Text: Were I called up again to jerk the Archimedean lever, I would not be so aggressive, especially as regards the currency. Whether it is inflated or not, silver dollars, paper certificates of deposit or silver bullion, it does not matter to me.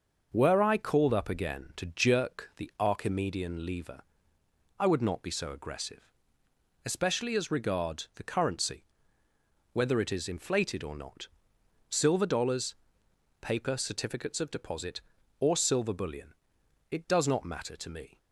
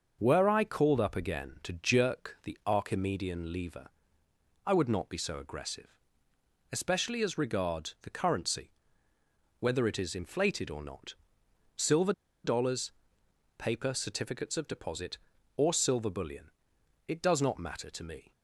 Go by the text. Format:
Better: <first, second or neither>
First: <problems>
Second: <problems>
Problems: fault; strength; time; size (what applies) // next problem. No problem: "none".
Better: first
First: starts louder than the rest; noticeable; until 1.3 s; 6 dB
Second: starts louder than the rest; noticeable; until 1.2 s; 6 dB // pauses between "silver" and "dollars"; slight; at 12.1 s; 0.32 s long